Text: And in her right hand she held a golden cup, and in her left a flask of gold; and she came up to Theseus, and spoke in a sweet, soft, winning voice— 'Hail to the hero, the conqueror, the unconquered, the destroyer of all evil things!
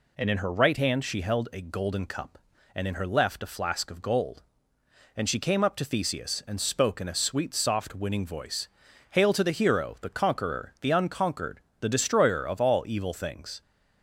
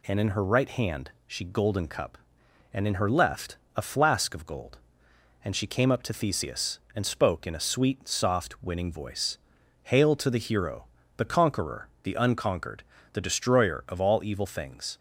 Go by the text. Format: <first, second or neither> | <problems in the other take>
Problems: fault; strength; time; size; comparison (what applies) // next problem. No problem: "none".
first | pauses between "hand" and "she"; slight; at 1.1 s; 0.16 s long // skips "held a"; at 1.4 s // pauses between "left" and "a"; slight; at 3.5 s; 0.18 s long